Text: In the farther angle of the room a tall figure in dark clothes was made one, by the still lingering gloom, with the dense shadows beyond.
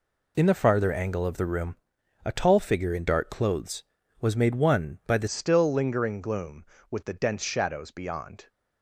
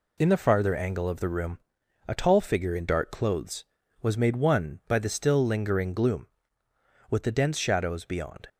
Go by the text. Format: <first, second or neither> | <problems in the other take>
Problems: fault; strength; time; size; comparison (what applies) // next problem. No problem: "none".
second | pauses between "room" and "a"; noticeable; at 1.7 s; 0.48 s long; noticeable in the second // changes voice at "still"; from 5.2 s on; 3.2 s long